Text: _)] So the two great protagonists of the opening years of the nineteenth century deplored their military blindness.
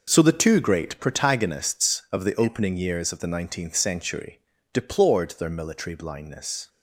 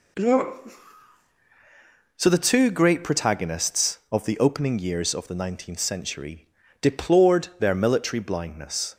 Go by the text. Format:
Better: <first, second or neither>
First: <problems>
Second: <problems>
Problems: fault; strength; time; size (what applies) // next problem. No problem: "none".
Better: neither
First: pauses between "century" and "deplored"; slight; at 4.3 s; 0.34 s long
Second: pauses between "century" and "deplored"; slight; at 6.4 s; 0.32 s long